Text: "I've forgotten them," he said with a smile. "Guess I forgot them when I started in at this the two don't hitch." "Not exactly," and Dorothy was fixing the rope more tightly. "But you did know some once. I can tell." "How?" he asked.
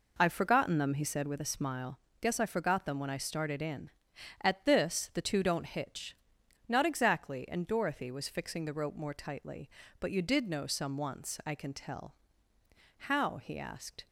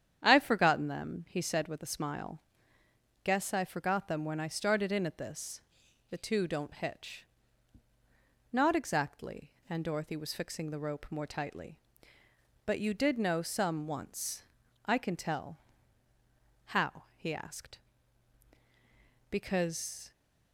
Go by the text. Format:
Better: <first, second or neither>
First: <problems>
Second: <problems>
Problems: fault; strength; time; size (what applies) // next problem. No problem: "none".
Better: first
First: none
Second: starts louder than the rest; strong; until 1.2 s; 9 dB // pauses between "this" and "the"; noticeable; at 5.5 s; 0.50 s long // goes on to say "Because"; noticeable; from 19.2 s on; 0.82 s long